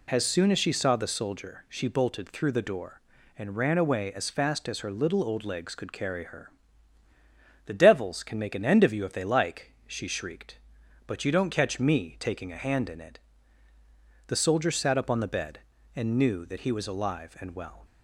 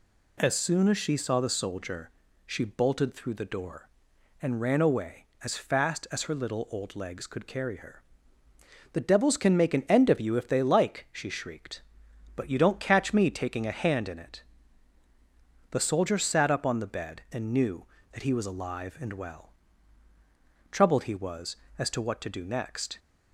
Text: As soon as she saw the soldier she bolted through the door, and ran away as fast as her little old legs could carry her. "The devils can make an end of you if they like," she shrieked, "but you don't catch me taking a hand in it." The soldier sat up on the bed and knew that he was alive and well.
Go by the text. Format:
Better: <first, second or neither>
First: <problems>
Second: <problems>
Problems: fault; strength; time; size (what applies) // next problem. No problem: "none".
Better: first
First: none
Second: pauses between "soldier" and "she"; slight; at 2.1 s; 0.36 s long // goes on to say "Troubled he was as to what to do next"; strong; from 20.7 s on; 2.2 s long